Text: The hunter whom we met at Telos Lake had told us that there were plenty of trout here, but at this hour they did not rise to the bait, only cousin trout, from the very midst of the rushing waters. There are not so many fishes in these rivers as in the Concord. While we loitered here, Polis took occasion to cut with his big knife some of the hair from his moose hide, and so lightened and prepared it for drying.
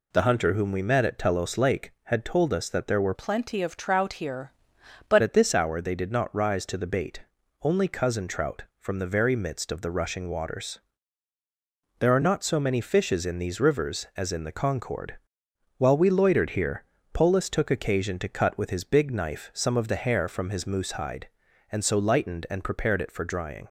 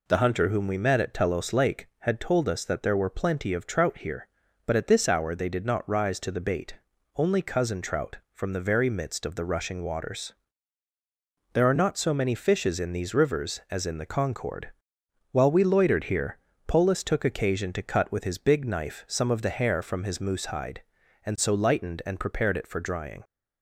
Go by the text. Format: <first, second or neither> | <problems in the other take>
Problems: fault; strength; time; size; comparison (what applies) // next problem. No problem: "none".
second | changes voice from "plenty" to "but"; from 3.1 to 5.2 s; 2.1 s long